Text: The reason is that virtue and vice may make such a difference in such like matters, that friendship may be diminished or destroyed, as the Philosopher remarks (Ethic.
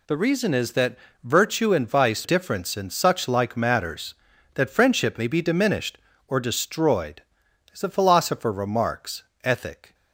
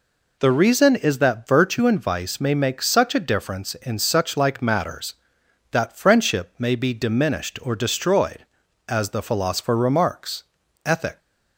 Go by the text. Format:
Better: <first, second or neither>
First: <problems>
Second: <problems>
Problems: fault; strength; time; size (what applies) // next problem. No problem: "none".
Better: second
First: pauses between "that" and "virtue"; slight; at 0.9 s; 0.26 s long // skips "may make such a"; at 2.2 s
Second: none